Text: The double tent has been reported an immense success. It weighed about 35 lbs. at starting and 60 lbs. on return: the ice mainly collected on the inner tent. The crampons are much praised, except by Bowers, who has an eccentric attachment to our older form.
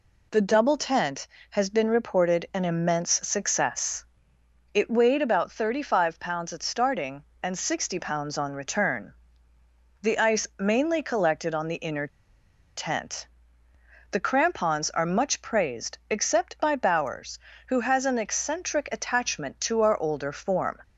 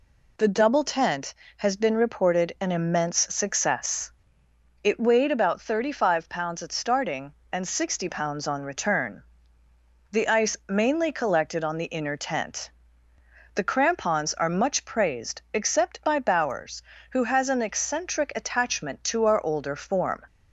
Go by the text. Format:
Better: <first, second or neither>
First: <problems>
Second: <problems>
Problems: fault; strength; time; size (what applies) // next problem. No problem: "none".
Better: second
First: pauses between "immense" and "success"; slight; at 3.1 s; 0.16 s long // pauses between "inner" and "tent"; noticeable; at 12.0 s; 0.68 s long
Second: pauses between "immense" and "success"; slight; at 3.1 s; 0.16 s long